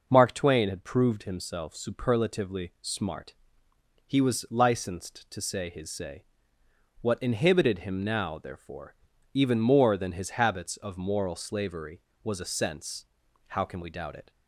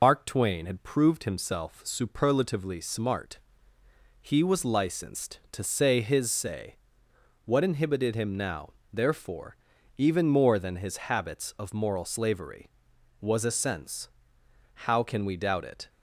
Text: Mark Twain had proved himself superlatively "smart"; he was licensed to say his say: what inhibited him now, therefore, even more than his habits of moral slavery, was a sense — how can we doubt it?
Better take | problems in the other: first | loses the start of "Mark"; at 0.0 s; 95 ms

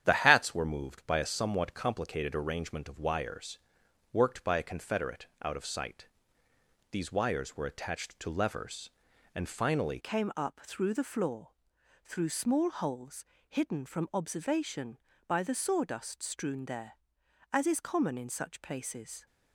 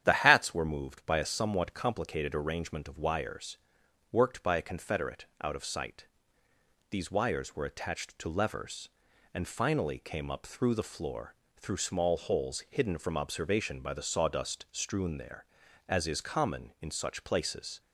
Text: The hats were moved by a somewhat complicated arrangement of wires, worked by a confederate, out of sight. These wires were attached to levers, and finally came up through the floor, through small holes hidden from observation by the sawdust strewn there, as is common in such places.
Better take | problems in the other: second | starts louder than the rest; strong; until 1.0 s; 9.5 dB; strong in the second // changes voice at "came"; from 9.9 s on; 9.3 s long // pauses between "holes" and "hidden"; slight; at 13.2 s; 0.24 s long

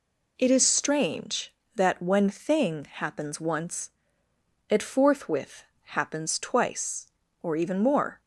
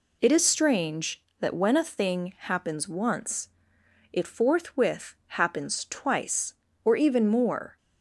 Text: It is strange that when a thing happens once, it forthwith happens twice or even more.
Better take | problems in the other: second | skips "a"; at 2.2 s // pauses between "forthwith" and "happens"; slight; at 5.6 s; 0.20 s long

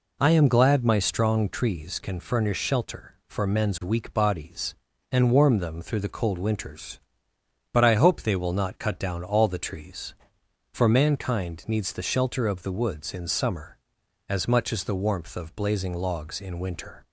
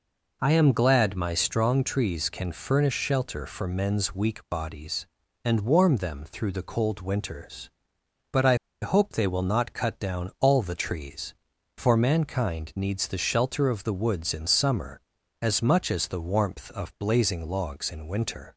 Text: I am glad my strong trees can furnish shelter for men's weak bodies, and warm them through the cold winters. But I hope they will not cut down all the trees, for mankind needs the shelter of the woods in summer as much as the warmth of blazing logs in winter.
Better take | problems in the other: first | pauses between "I" and "hope"; slight; at 8.5 s; 0.25 s long

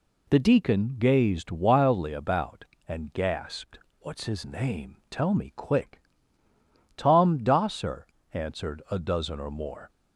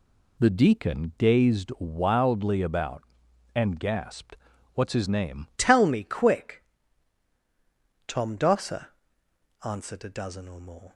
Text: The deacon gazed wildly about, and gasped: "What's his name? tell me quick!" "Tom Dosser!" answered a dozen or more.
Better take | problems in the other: first | changes voice at "tell"; from 5.5 s on; 5.4 s long

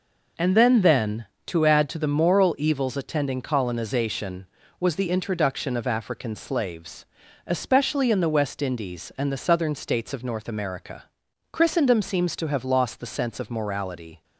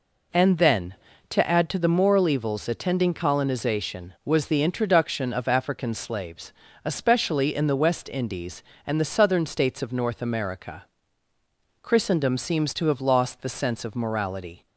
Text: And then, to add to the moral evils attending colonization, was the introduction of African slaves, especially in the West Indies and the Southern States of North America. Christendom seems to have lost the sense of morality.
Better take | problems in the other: second | says "then" twice; at 0.8 s

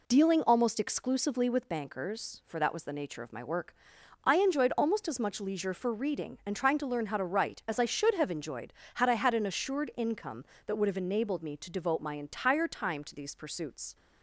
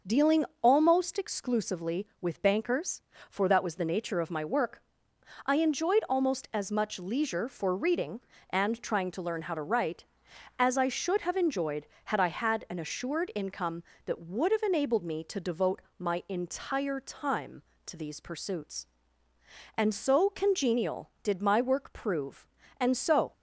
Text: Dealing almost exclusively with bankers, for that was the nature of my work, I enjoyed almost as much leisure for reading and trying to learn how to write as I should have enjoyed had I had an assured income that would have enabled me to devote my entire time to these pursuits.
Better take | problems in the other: first | starts louder than the rest; until 1.2 s; 6 dB // pauses between "Dealing" and "almost"; slight; at 0.4 s; 0.18 s long // pauses between "devote" and "my"; slight; at 15.8 s; 0.18 s long // goes on to say "And so congenial did my work prove and so"; strong; from 19.7 s on; 3.5 s long

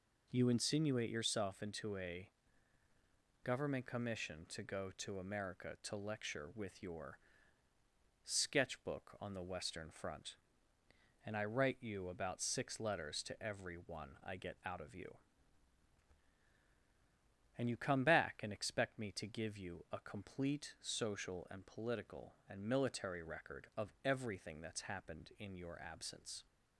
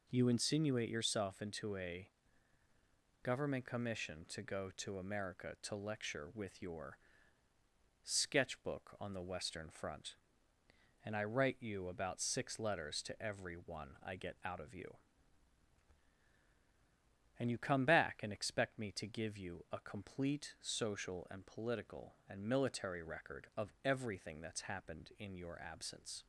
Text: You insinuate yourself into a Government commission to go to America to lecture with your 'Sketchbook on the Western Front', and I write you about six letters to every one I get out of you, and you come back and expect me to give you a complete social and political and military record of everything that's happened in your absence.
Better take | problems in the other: neither | pauses between "a" and "Government"; the same in both // pauses between "your" and "Sketchbook"; the same in both

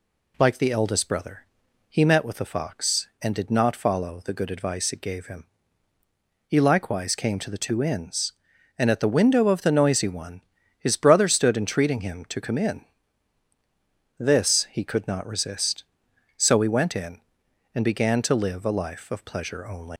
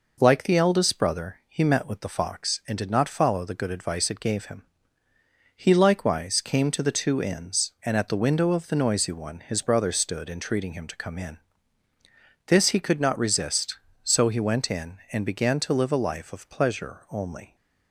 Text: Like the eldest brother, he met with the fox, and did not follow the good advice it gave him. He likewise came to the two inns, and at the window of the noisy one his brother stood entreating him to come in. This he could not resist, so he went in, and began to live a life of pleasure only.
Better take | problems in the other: second | pauses between "one" and "his"; slight; at 10.4 s; 0.36 s long // leaves "only" unfinished; at 19.9 s; 145 ms

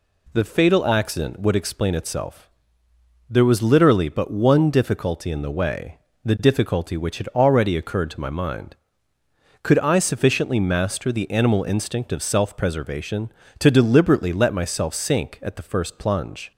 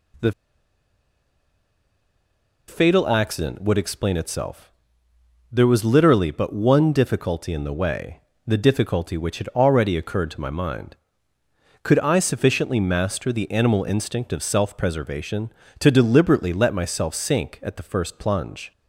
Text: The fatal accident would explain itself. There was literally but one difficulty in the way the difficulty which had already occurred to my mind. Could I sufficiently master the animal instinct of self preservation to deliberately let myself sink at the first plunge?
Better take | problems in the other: first | pauses between "The" and "fatal"; strong; at 0.3 s; 2.3 s long // pauses between "way" and "the"; slight; at 8.1 s; 0.26 s long; slight in the first

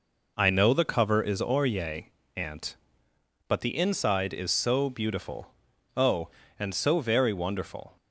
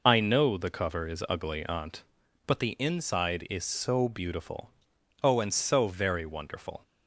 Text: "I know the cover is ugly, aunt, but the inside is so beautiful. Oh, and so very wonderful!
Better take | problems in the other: second | says "orye" for "ugly"; at 1.4 s

